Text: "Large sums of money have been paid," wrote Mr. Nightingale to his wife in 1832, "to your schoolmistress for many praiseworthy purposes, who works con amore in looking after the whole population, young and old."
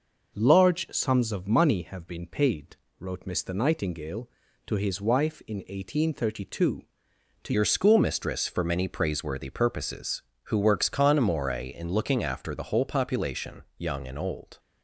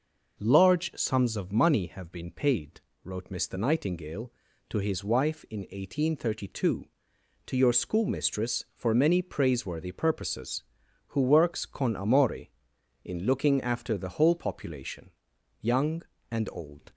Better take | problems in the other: second | changes voice at "your"; from 7.5 s on; 7.0 s long

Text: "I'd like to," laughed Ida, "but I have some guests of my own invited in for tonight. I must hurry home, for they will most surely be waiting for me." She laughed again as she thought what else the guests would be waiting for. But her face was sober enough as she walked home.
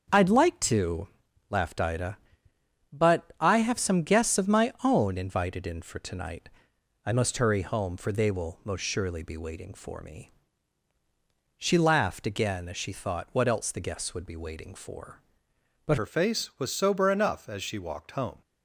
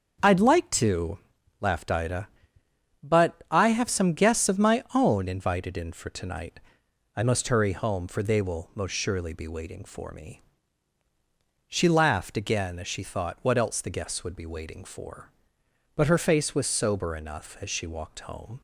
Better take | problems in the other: second | starts louder than the rest; until 1.5 s; 7 dB; also in the second // changes voice at "her"; from 15.9 s on; 2.5 s long

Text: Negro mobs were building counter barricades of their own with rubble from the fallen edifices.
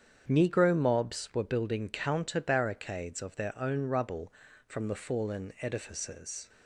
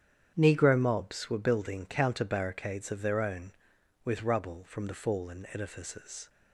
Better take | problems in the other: second | starts louder than the rest; strong; until 1.2 s; 8 dB; strong in the second // skips "with"; at 3.8 s

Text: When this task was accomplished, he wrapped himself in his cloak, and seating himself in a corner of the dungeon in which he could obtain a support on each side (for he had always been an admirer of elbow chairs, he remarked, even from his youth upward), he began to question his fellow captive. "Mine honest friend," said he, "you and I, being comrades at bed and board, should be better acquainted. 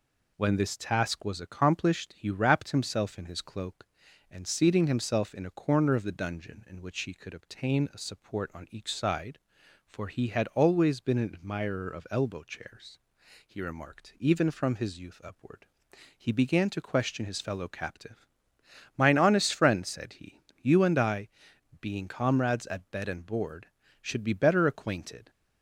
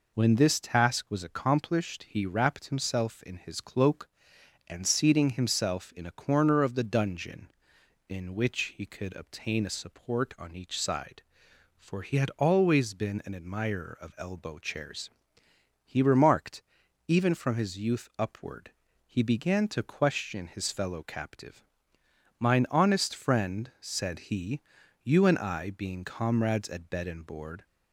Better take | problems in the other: first | stops before "should be better acquainted"; at 27.6 s

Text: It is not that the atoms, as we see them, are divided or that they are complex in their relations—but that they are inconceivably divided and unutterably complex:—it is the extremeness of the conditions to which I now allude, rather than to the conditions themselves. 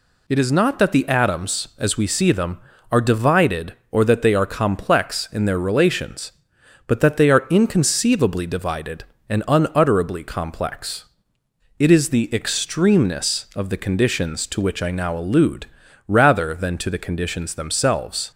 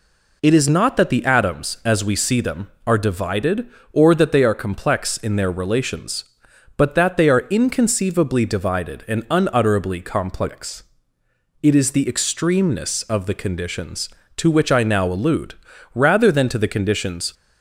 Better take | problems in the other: first | stops before "themselves"; at 17.3 s

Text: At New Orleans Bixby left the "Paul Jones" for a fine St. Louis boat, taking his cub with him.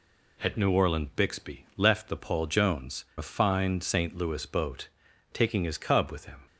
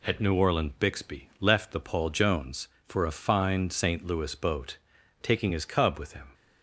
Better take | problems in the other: second | skips "for"; at 3.1 s

